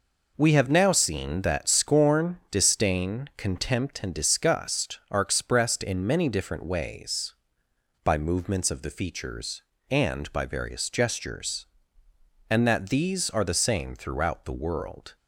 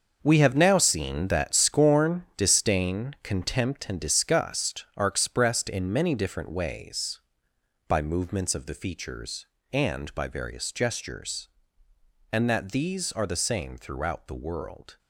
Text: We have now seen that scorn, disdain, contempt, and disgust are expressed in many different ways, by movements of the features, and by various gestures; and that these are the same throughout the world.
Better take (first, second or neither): first